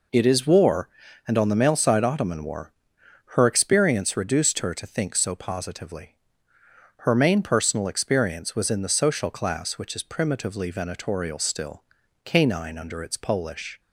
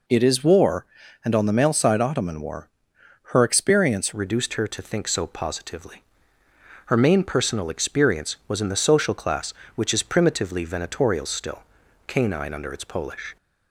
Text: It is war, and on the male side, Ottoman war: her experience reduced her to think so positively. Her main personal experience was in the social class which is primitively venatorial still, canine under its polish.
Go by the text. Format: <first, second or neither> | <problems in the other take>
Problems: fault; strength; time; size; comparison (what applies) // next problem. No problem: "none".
first | changes voice at "reduced"; from 4.1 s on; 9.2 s long